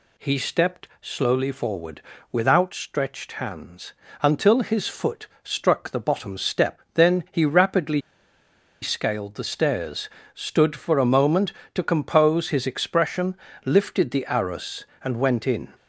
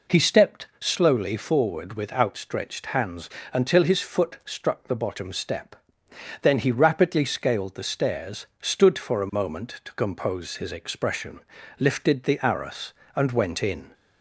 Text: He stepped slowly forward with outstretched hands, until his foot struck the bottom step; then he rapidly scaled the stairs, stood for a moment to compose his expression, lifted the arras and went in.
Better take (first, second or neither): second